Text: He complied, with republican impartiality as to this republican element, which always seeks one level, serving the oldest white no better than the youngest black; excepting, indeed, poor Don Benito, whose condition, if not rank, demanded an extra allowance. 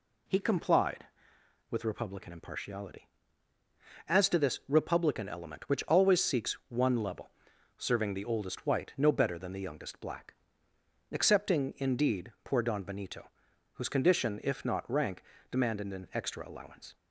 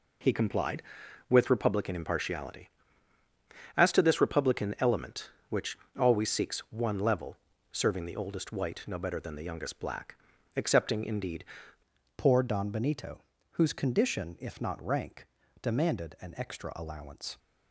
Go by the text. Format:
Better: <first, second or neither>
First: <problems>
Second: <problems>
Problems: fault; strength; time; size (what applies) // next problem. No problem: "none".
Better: first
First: none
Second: pauses between "which" and "always"; slight; at 5.7 s; 0.22 s long // changes voice at "poor"; from 12.1 s on; 5.2 s long